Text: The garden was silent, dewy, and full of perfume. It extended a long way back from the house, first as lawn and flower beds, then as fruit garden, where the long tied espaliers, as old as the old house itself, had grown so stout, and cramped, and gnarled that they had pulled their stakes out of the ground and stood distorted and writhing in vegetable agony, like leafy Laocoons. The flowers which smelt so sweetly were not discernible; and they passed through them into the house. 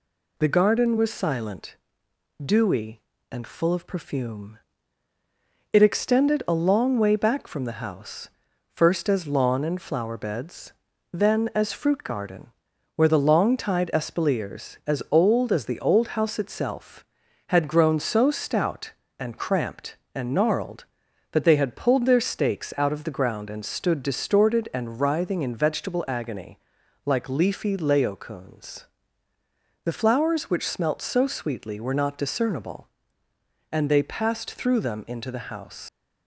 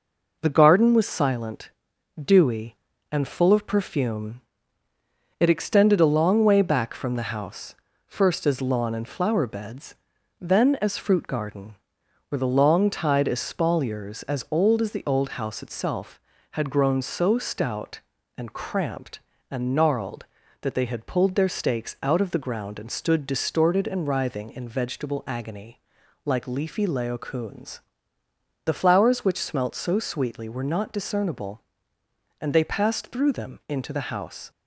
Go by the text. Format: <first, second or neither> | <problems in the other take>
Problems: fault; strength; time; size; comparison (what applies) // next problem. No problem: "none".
second | leaves "house" unfinished; at 35.8 s; 105 ms